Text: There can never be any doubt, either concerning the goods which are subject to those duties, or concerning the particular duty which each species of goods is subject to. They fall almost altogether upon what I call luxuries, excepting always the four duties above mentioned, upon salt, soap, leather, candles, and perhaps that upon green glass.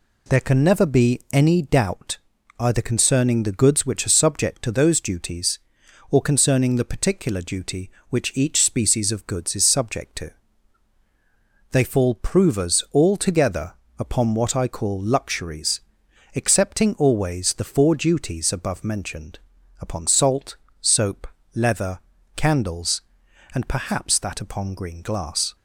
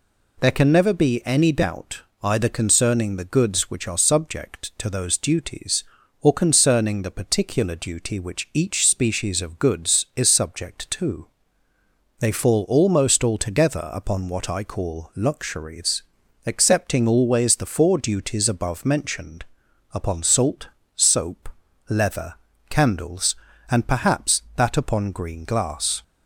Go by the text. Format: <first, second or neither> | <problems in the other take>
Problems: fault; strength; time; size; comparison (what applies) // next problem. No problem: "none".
second | says "provers" for "almost"; at 12.1 s // pauses between "altogether" and "upon"; slight; at 13.7 s; 0.24 s long